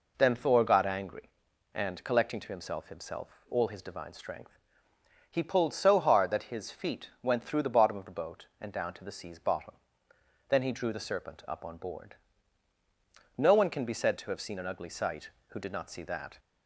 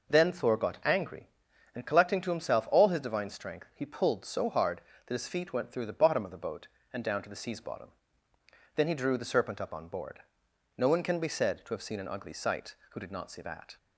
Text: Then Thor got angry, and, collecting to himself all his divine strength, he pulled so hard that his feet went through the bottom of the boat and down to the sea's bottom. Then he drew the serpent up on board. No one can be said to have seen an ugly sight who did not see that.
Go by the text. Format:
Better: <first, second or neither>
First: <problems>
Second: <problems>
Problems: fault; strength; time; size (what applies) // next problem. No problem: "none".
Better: second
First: says "himself" twice; at 2.8 s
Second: none